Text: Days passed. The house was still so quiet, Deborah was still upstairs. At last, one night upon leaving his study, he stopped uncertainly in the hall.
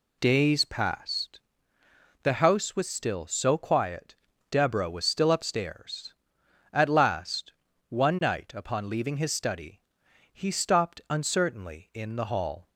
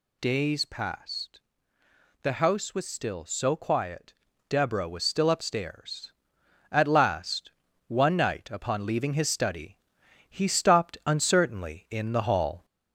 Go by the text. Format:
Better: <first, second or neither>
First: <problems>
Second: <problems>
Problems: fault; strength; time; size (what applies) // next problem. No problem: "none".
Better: first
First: none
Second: gets louder; slight; throughout; 2 dB